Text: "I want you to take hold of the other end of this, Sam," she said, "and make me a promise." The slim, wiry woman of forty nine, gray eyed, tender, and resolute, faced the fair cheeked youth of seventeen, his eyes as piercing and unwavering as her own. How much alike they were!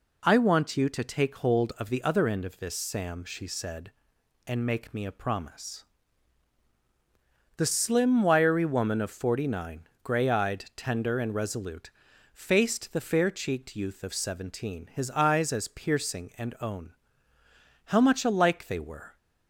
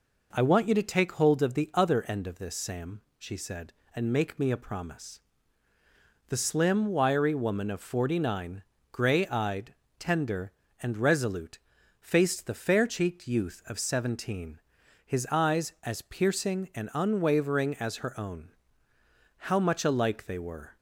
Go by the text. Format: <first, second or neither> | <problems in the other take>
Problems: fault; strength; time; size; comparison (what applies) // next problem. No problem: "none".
second | skips "unwavering as her"; at 16.5 s